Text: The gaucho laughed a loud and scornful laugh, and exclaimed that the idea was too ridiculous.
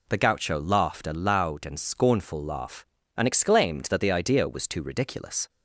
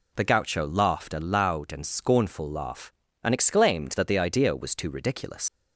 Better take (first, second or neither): first